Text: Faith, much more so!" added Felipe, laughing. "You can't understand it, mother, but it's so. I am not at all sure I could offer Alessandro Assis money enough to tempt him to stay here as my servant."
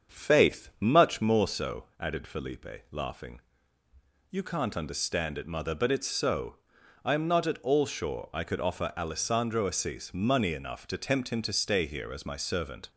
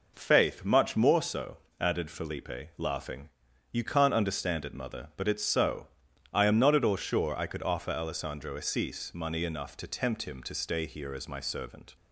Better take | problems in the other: second | starts louder than the rest; strong; until 1.3 s; 7 dB

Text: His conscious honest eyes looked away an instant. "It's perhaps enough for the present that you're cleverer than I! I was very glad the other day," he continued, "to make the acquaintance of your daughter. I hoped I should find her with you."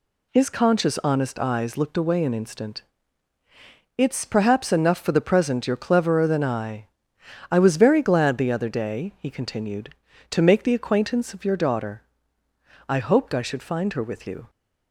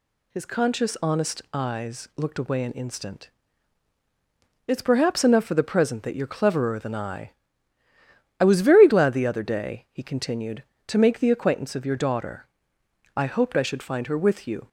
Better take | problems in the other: second | skips "that"; at 5.6 s

